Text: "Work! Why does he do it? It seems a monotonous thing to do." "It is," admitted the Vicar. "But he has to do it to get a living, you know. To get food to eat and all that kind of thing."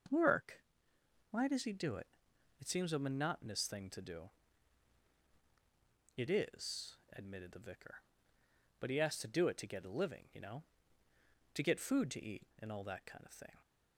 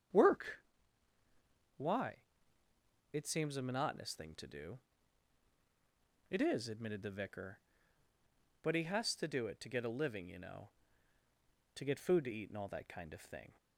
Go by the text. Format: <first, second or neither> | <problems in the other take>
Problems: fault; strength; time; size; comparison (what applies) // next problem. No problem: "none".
first | starts louder than the rest; strong; until 3.2 s; 8 dB // skips "does he do it"; at 2.6 s